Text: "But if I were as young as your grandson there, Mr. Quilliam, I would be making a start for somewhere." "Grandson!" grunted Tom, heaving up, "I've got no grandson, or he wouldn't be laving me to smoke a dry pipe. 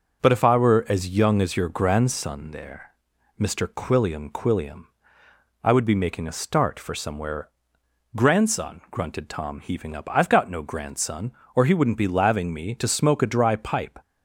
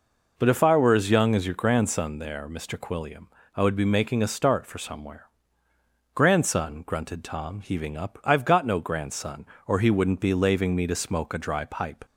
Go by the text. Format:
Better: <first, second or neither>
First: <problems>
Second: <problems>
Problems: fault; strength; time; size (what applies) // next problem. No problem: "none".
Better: second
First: says "Quilliam" twice; at 4.2 s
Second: none